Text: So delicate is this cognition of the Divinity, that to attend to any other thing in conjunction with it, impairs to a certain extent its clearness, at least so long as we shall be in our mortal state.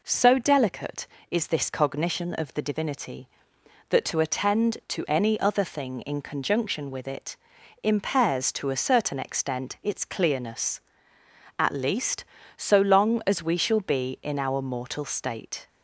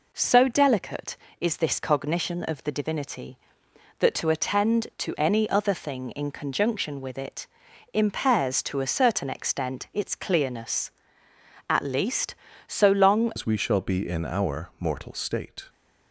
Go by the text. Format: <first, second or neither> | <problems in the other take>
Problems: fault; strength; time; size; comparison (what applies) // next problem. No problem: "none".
first | changes voice at "as"; from 13.3 s on; 2.3 s long